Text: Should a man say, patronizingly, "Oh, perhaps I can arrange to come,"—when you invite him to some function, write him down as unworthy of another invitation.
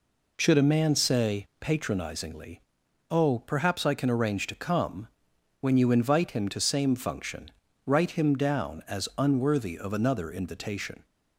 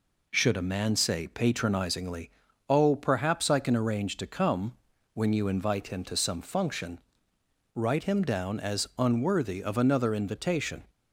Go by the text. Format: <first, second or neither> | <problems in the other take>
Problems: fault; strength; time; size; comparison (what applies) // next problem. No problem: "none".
second | says "same" for "some"; at 6.6 s